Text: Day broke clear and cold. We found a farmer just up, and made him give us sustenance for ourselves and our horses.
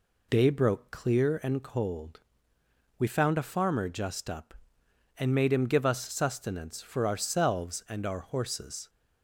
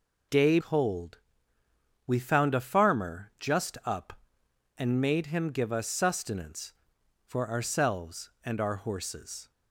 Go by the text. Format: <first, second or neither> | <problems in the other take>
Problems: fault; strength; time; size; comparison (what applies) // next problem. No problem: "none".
first | skips "broke clear and"; at 0.5 s